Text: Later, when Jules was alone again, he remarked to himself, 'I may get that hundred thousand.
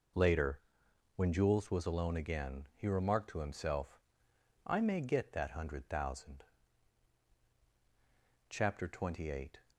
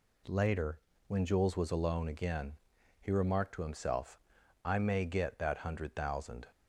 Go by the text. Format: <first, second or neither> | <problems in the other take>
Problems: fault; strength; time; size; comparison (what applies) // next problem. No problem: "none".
second | goes on to say "Chapter Twenty Eight"; noticeable; from 8.4 s on; 1.1 s long